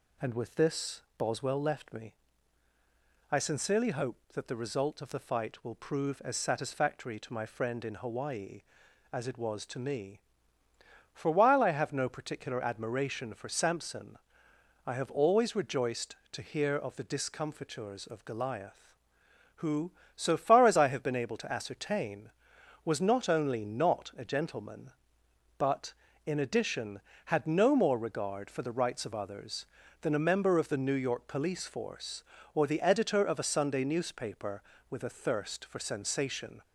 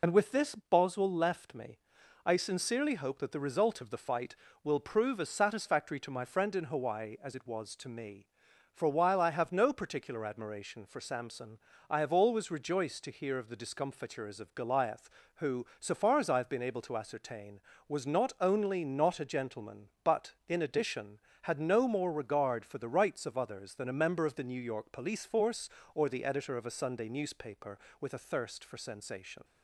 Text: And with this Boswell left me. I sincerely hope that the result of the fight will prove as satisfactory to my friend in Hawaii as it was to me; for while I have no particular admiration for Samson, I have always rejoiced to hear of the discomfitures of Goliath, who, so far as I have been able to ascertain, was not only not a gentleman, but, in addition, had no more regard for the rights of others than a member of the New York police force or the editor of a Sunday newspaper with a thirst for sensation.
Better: first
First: none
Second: loses the start of "And"; at 0.0 s; 45 ms

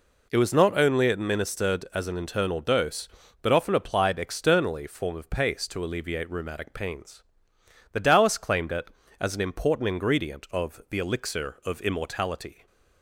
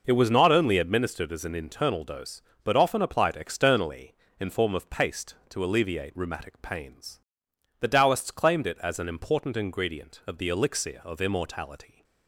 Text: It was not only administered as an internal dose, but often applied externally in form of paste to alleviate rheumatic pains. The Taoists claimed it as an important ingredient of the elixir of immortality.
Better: second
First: skips "in"; at 4.8 s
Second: none

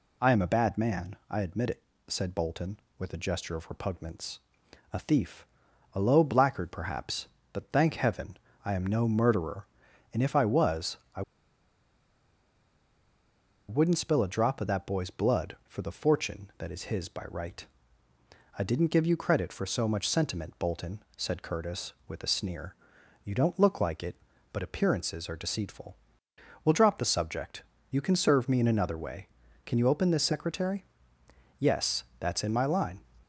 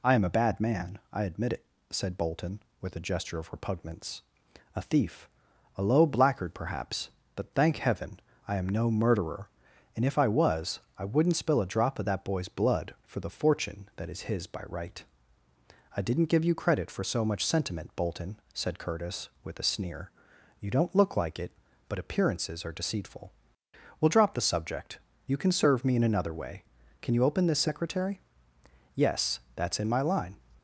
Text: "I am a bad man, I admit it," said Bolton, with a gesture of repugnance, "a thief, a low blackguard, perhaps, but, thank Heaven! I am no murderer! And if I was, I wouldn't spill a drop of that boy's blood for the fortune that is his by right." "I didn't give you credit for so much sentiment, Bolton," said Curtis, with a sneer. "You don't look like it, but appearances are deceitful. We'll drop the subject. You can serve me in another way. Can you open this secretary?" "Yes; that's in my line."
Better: second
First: pauses between "I" and "wouldn't"; strong; at 11.2 s; 2.4 s long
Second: none

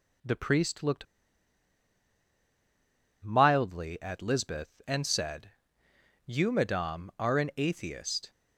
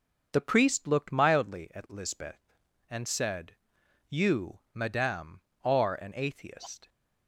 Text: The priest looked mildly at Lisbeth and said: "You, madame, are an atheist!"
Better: second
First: pauses between "looked" and "mildly"; strong; at 1.0 s; 2.1 s long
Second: none

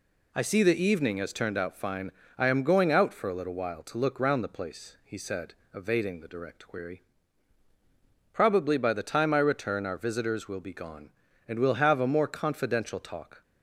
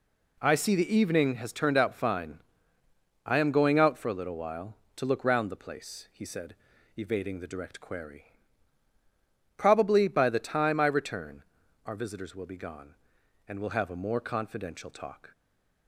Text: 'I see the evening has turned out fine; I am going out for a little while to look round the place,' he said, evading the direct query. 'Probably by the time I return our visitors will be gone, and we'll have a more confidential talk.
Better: first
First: none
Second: pauses between "return" and "our"; at 11.4 s; 0.44 s long // stays silent after the last word; slight; from 15.3 s on; 0.5 s long

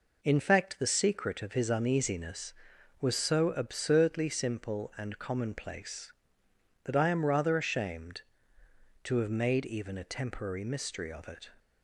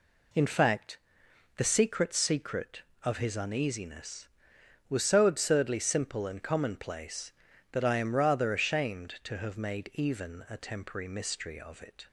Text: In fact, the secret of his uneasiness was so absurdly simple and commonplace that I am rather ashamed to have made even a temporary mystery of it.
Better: first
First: none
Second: says "secret" twice; at 2.1 s

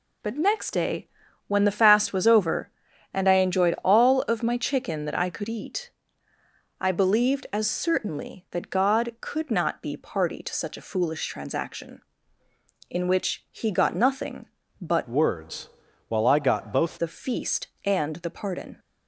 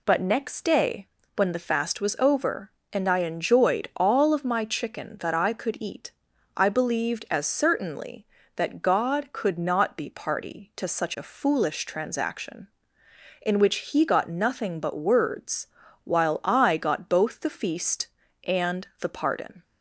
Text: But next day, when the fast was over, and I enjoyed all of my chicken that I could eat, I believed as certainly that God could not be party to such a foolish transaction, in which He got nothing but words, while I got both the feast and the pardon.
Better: second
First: changes voice from "words" to "both"; from 15.0 to 16.9 s; 1.9 s long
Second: none

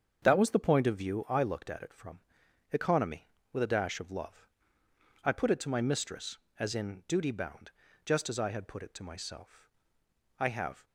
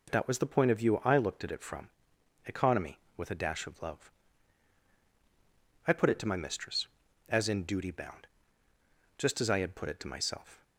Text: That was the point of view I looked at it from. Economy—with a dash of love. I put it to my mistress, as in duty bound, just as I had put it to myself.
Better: second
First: starts louder than the rest; strong; until 1.2 s; 7.5 dB // goes on to say "I have"; slight; from 10.3 s on; 0.46 s long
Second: none

